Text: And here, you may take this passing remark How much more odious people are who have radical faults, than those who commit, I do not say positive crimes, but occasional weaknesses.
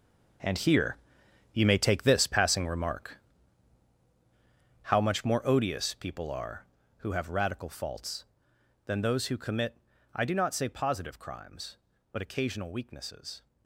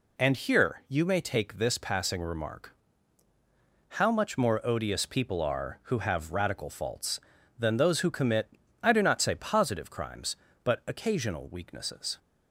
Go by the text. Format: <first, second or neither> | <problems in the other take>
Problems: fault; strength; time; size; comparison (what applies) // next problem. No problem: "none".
second | gets quieter; strong; throughout; 12.5 dB // pauses between "remark" and "How"; strong; at 3.1 s; 1.6 s long; also in the second